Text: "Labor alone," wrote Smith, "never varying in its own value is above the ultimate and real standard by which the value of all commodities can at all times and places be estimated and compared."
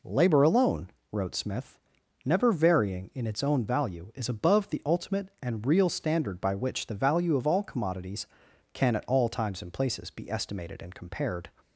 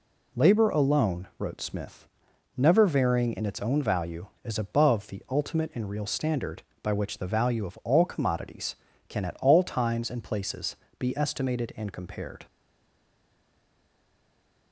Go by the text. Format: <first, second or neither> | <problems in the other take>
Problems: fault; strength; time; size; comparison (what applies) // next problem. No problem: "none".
first | pauses between "places" and "be"; slight; at 10.7 s; 0.22 s long // stays silent after the last word; from 12.4 s on; 2.3 s long